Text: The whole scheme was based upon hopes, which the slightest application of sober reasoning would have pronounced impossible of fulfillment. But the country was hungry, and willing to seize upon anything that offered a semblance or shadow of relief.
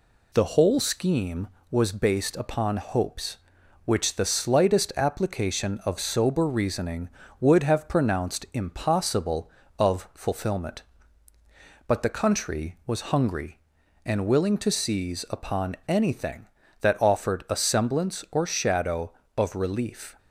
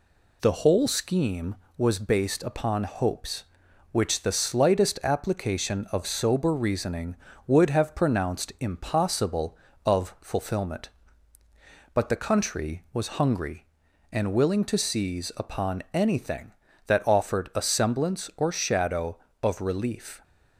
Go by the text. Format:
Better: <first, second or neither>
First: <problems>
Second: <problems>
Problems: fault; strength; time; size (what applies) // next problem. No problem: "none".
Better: neither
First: none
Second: none